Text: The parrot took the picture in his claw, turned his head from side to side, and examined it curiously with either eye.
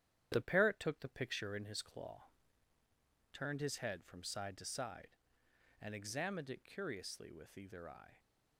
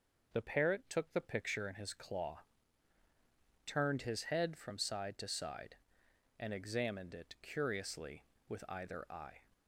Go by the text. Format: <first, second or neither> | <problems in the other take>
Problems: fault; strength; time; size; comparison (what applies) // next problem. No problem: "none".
second | gets quieter; noticeable; throughout; 4.5 dB